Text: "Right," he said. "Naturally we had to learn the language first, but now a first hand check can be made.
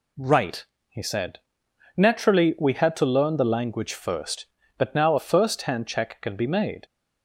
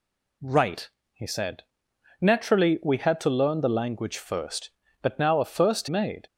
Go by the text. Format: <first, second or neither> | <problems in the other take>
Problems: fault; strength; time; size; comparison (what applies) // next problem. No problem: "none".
first | skips "hand check can be"; at 5.8 s